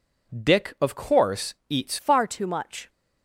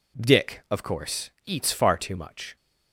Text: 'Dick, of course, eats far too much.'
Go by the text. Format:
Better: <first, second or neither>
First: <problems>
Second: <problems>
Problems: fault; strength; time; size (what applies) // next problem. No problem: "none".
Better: second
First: changes voice at "far"; from 1.9 s on; 0.9 s long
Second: none